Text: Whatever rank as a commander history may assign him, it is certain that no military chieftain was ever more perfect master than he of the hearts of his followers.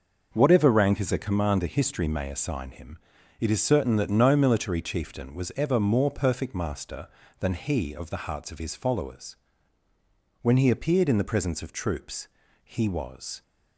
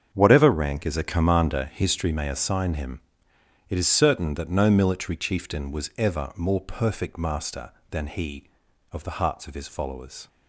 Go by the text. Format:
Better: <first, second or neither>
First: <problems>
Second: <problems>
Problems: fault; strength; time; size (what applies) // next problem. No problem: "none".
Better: second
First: starts louder than the rest; noticeable; until 1.3 s; 6 dB // goes on to say "When he appeared in the presence of troops he was"; strong; from 10.4 s on; 3.0 s long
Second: starts louder than the rest; strong; until 1.1 s; 7.5 dB